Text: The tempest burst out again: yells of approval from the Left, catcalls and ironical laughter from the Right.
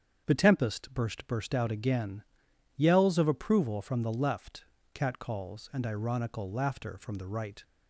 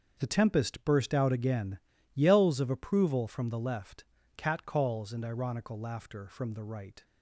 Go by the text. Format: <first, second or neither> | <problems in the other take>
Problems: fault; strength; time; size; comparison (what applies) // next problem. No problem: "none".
second | starts louder than the rest; strong; until 1.3 s; 7.5 dB; also in the second // says "burst" twice; at 1.2 s